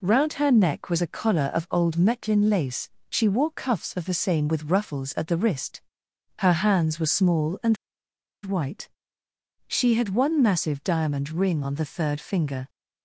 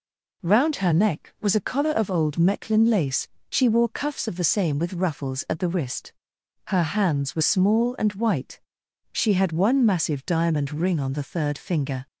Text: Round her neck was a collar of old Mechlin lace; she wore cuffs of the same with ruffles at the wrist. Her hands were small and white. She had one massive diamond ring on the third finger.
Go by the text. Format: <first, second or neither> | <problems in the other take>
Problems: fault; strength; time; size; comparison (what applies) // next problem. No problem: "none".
second | pauses between "and" and "white"; noticeable; at 7.7 s; 0.68 s long